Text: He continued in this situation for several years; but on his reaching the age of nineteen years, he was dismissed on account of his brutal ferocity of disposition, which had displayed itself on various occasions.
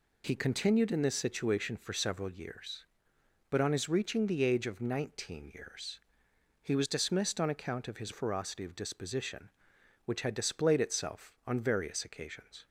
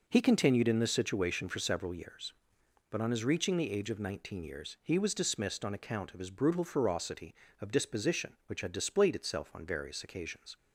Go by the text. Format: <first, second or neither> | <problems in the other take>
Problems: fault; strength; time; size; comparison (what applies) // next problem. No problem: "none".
second | skips "brutal"; at 8.1 s